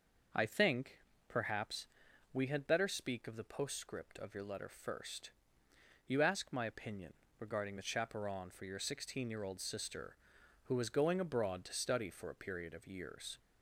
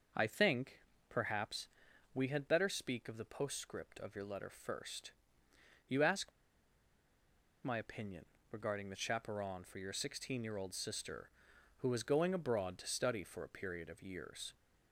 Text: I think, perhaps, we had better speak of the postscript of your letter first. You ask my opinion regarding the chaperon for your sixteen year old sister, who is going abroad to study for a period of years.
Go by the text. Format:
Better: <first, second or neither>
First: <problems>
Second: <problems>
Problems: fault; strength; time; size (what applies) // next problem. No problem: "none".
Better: first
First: starts louder than the rest; noticeable; until 1.6 s; 6 dB // pauses between "opinion" and "regarding"; slight; at 7.1 s; 0.26 s long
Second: starts louder than the rest; noticeable; until 1.4 s; 6 dB // pauses between "ask" and "my"; strong; at 6.3 s; 1.3 s long // pauses between "opinion" and "regarding"; slight; at 8.2 s; 0.26 s long